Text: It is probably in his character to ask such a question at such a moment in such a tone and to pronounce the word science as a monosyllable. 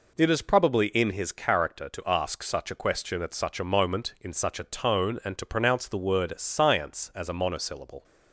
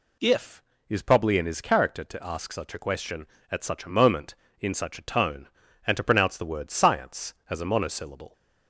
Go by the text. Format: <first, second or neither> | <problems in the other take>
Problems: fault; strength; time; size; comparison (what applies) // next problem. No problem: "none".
first | says "If" for "It"; at 0.1 s